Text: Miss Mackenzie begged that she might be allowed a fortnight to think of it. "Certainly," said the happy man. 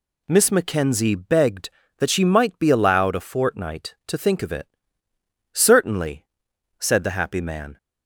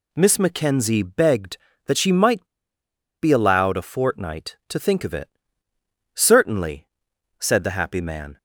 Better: first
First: none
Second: pauses between "might" and "be"; noticeable; at 2.4 s; 0.75 s long

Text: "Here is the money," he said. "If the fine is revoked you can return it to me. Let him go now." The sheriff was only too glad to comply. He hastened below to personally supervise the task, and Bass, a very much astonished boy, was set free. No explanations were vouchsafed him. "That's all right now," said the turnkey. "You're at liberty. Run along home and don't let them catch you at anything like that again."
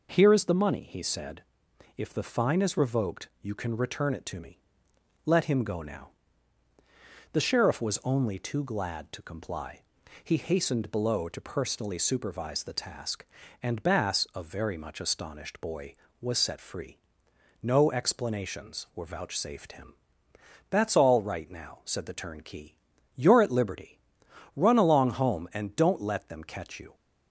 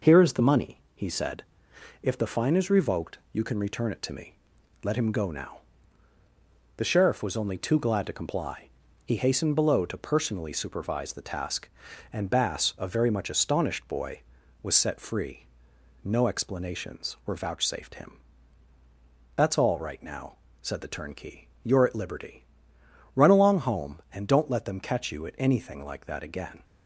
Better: second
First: stops before "at anything like that again"; at 26.9 s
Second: none

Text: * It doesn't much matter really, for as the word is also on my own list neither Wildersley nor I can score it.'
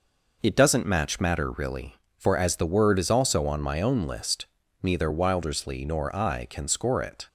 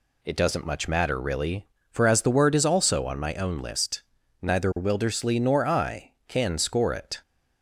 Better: second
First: says "match" for "much"; at 0.8 s // pauses between "list" and "neither"; slight; at 4.4 s; 0.36 s long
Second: pauses between "list" and "neither"; at 4.0 s; 0.42 s long

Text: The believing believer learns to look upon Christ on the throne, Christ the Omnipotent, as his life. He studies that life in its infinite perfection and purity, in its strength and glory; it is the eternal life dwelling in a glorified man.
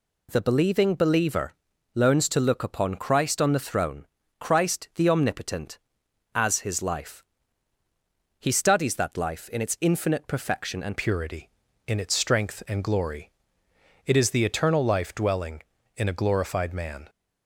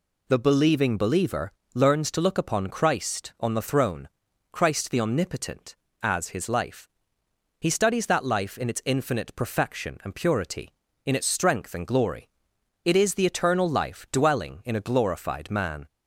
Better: second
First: pauses between "believer" and "learns"; at 1.5 s; 0.42 s long // changes voice at "purity"; from 10.9 s on; 6.1 s long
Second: pauses between "believer" and "learns"; slight; at 1.5 s; 0.20 s long

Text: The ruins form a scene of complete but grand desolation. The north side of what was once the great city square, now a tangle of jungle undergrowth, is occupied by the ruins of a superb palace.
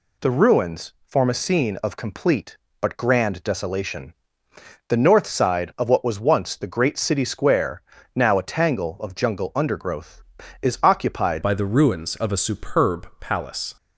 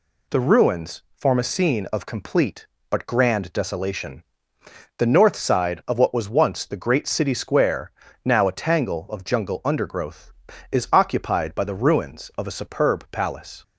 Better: second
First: changes voice at "by"; from 11.4 s on; 2.3 s long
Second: none

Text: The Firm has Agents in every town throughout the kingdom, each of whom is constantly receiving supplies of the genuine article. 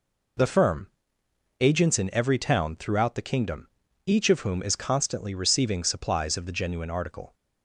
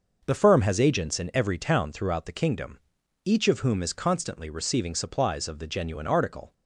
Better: second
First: skips "has"; at 1.2 s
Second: none

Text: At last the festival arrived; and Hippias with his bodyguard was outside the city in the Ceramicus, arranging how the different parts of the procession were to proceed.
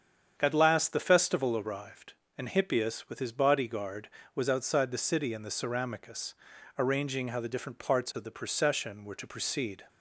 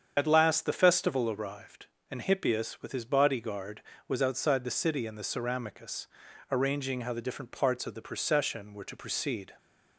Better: first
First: starts louder than the rest; strong; until 1.3 s; 8 dB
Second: loses the start of "At"; at 0.1 s; 60 ms // starts louder than the rest; strong; until 1.1 s; 7.5 dB

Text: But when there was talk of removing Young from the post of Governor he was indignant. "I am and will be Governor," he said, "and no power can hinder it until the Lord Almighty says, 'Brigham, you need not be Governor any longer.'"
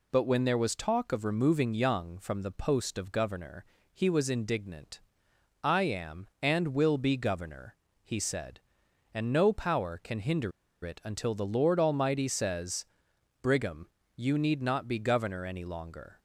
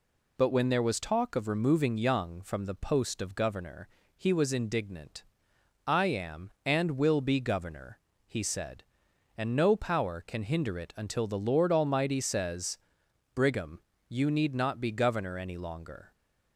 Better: second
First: pauses between "Governor" and "he"; slight; at 3.6 s; 0.28 s long // pauses between "hinder" and "it"; slight; at 10.5 s; 0.33 s long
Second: pauses between "Governor" and "he"; slight; at 3.8 s; 0.28 s long

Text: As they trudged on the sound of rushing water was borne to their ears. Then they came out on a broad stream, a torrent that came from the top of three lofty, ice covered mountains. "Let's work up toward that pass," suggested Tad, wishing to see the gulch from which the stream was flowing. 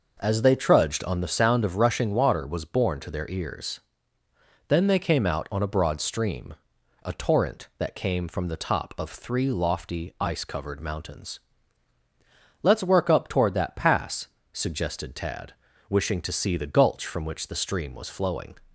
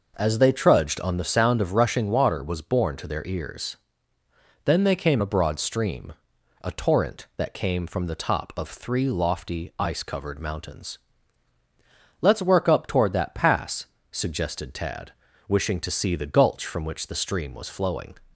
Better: first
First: none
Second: skips "out on"; at 5.2 s

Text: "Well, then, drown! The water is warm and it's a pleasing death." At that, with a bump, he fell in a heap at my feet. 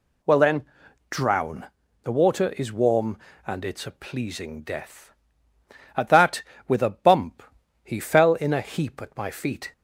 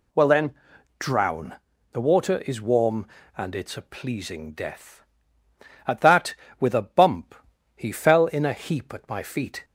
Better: neither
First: none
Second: none

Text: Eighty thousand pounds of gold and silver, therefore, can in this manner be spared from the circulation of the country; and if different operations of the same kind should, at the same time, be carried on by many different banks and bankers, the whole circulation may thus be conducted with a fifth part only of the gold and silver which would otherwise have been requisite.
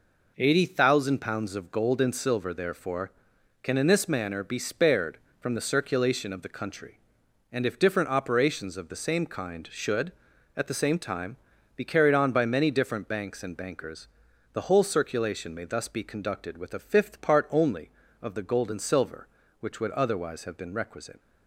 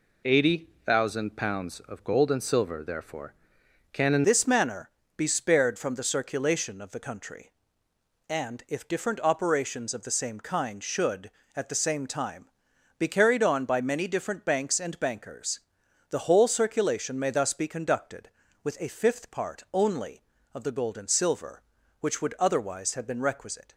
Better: first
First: none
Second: pauses between "Eighty" and "thousand"; slight; at 0.6 s; 0.16 s long // changes voice at "this"; from 4.2 s on; 19.5 s long // pauses between "manner" and "be"; slight; at 4.8 s; 0.28 s long

